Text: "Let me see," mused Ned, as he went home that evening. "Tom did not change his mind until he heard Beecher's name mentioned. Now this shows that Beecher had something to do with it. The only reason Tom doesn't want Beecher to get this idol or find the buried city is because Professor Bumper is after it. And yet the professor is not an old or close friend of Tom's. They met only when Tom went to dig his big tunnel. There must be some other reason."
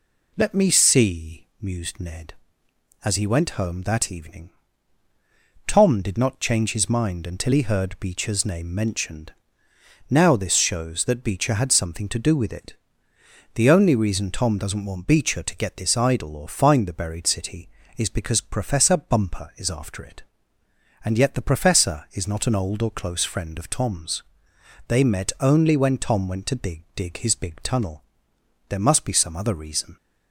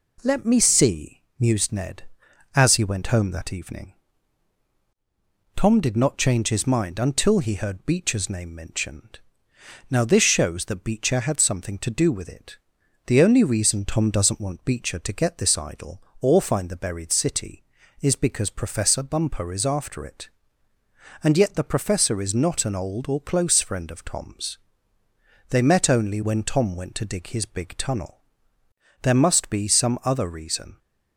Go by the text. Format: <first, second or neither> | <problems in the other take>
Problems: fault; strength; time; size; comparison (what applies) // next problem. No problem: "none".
second | says "dig" twice; at 26.9 s